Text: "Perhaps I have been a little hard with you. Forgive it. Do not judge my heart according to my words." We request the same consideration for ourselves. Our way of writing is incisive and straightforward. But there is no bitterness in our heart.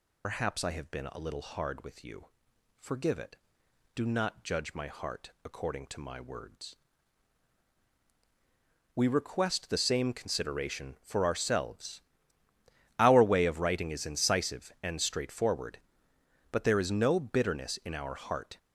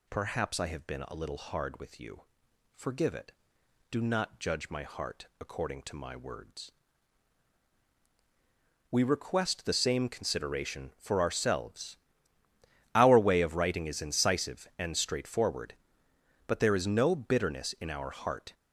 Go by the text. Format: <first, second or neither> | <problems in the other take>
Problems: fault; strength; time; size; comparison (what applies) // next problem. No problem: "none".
second | loses the start of "Perhaps"; at 0.2 s; 110 ms